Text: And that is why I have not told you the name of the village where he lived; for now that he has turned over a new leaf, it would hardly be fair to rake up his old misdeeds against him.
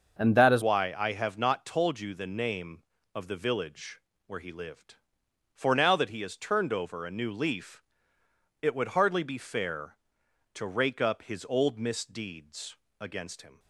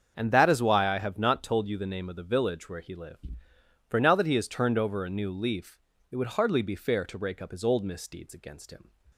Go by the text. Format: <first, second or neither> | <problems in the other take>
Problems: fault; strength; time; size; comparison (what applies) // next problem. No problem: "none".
second | starts louder than the rest; until 1.2 s; 6.5 dB; also in the second // changes voice at "why"; from 0.6 s on; 12.9 s long // pauses between "village" and "where"; slight; at 4.0 s; 0.26 s long // pauses between "misdeeds" and "against"; slight; at 12.7 s; 0.22 s long